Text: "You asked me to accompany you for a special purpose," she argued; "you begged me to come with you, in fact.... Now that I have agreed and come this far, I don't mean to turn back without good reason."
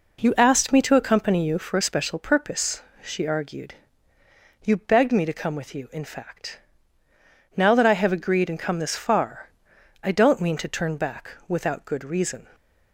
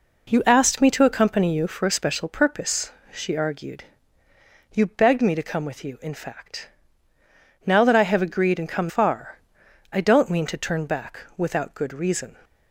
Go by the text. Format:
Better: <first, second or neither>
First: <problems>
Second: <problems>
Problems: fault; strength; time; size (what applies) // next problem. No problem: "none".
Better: first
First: pauses between "back" and "without"; slight; at 11.3 s; 0.16 s long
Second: skips "this"; at 8.8 s // pauses between "back" and "without"; slight; at 11.1 s; 0.16 s long